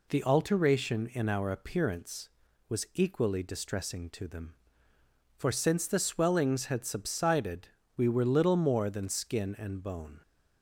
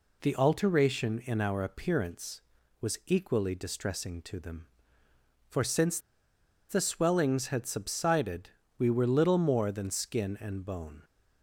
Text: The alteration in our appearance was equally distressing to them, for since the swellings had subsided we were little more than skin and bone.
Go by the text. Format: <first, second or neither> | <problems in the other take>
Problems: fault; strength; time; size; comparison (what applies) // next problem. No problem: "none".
first | pauses between "since" and "the"; noticeable; at 5.9 s; 0.71 s long // pauses between "subsided" and "we"; slight; at 8.4 s; 0.30 s long; slight in the first